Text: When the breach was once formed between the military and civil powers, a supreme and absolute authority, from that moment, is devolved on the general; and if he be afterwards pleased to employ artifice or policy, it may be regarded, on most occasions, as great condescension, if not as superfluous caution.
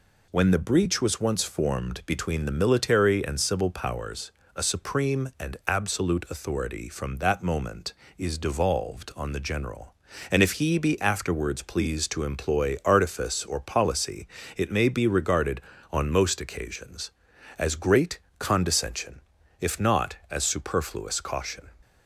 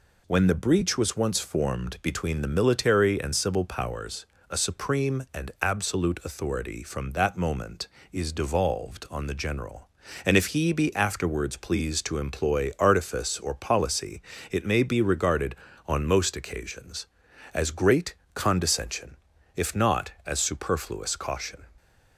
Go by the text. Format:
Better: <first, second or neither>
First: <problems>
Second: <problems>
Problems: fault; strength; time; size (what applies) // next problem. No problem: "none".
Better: neither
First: pauses between "great" and "condescension"; slight; at 18.1 s; 0.18 s long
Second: pauses between "great" and "condescension"; slight; at 18.1 s; 0.18 s long